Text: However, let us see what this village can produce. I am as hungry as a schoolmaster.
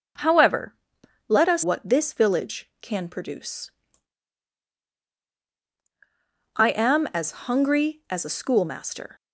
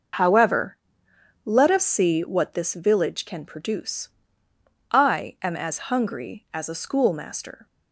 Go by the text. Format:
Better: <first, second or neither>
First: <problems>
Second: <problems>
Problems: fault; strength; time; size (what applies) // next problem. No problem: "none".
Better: second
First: starts louder than the rest; until 1.7 s; 6.5 dB // skips "see"; at 1.6 s // pauses between "as" and "hungry"; slight; at 7.3 s; 0.16 s long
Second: starts louder than the rest; noticeable; until 1.8 s; 6 dB